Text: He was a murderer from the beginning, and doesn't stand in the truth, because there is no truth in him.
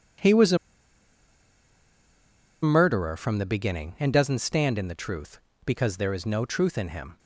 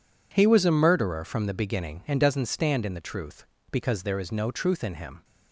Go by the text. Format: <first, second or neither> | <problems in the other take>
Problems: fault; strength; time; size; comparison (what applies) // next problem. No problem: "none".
second | pauses between "a" and "murderer"; strong; at 0.5 s; 2.0 s long